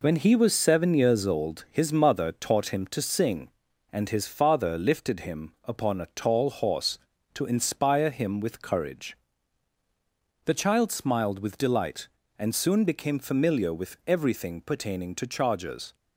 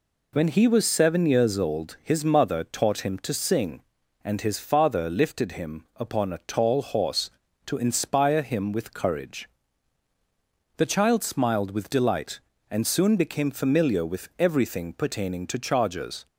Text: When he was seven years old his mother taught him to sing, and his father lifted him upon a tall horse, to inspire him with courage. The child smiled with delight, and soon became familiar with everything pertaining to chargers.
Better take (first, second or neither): second